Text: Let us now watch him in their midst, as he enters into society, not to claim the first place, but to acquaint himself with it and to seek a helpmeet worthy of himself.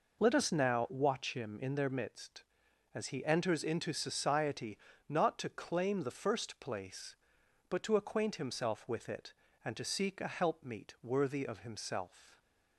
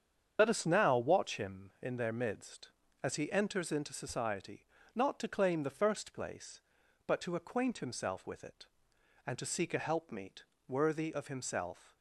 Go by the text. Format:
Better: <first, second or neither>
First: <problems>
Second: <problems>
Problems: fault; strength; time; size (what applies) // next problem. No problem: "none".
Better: first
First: none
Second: loses the start of "Let"; at 0.3 s; 50 ms // starts louder than the rest; strong; until 1.4 s; 7.5 dB // pauses between "helpmeet" and "worthy"; slight; at 10.4 s; 0.24 s long